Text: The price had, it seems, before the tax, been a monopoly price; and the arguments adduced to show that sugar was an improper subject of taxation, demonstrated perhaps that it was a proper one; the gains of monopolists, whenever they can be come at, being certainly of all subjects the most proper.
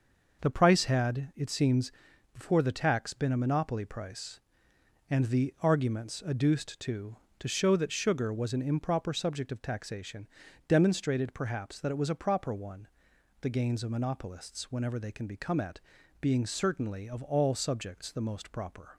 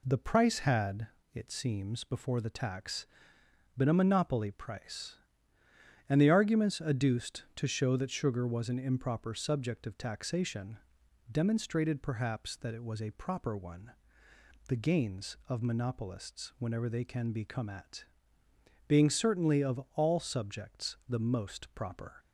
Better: second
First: says "to" twice; at 7.3 s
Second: none

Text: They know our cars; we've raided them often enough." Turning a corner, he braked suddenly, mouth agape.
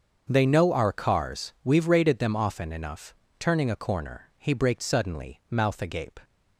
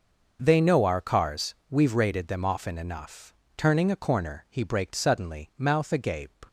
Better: neither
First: starts louder than the rest; until 1.3 s; 6.5 dB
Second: starts louder than the rest; noticeable; until 1.4 s; 6 dB

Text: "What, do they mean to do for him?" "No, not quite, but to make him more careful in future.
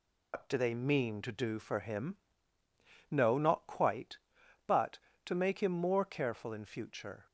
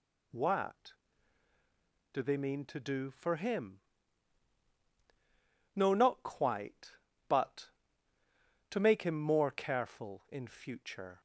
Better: second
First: loses the start of "What"; at 0.3 s; 135 ms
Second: none

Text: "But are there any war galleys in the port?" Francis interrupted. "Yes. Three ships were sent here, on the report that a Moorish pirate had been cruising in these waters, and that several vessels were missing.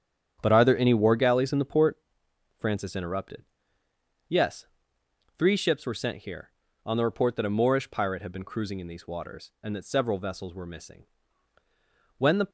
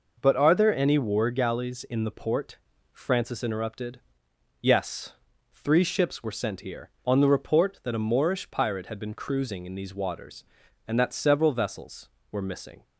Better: second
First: starts louder than the rest; strong; until 1.4 s; 8.5 dB // goes on to say "When the"; slight; from 12.1 s on; 0.32 s long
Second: none

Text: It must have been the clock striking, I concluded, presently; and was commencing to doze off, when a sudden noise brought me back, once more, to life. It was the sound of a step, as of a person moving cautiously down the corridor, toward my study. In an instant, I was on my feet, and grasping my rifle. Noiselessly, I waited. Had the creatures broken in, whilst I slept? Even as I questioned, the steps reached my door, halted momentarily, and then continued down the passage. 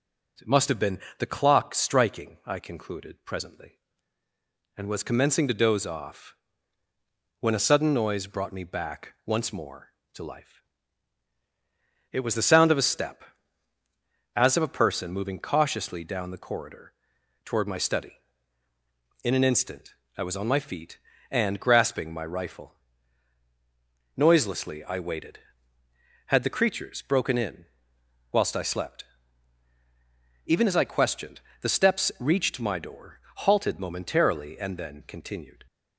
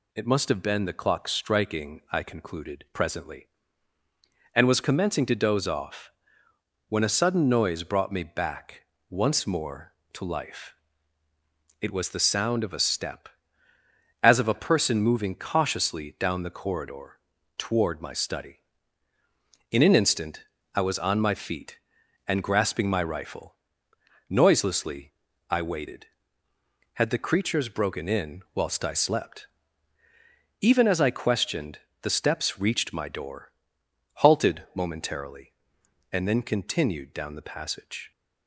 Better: second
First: starts louder than the rest; until 1.5 s; 6 dB // pauses between "been" and "the"; slight; at 1.0 s; 0.18 s long // stops before "down the passage"; at 35.6 s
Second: none

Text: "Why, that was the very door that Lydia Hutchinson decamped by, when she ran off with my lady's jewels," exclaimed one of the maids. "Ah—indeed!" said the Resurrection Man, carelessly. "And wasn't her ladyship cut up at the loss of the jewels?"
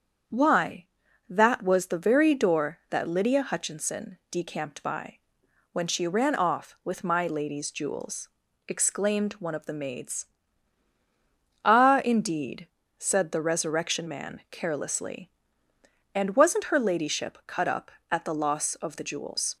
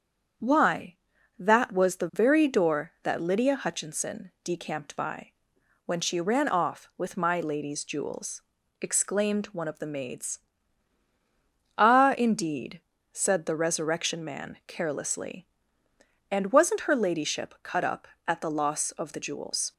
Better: neither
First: starts louder than the rest; strong; until 1.7 s; 7.5 dB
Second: starts louder than the rest; strong; until 1.8 s; 7.5 dB

